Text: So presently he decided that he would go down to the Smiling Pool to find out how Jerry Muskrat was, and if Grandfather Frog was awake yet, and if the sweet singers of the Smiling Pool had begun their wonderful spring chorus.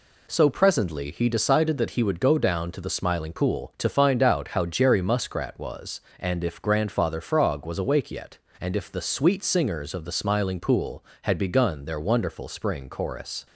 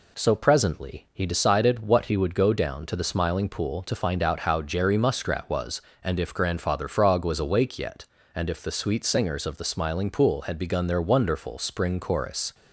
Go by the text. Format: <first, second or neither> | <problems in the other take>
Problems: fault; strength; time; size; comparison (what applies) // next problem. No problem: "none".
first | says "what" for "that"; at 1.8 s